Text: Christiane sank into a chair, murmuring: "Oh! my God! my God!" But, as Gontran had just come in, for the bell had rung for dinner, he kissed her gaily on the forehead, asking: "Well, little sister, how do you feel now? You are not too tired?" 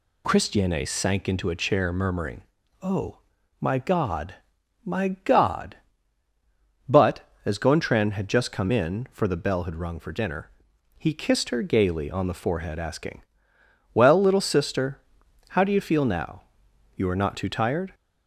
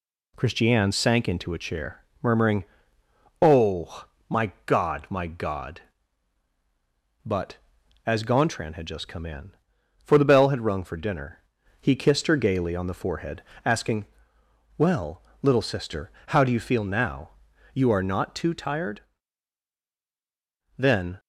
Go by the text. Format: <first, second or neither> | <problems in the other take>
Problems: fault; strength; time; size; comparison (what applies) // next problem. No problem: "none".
first | goes on to say "Then"; slight; from 20.7 s on; 0.42 s long